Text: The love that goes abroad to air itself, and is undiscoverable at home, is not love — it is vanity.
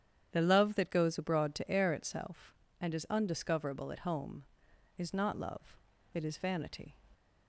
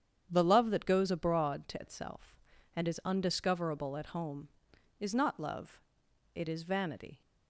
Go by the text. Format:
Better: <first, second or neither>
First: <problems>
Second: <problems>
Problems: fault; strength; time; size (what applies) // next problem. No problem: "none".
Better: first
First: starts louder than the rest; strong; until 1.3 s; 9 dB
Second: starts louder than the rest; strong; until 1.3 s; 8.5 dB // skips "air"; at 1.8 s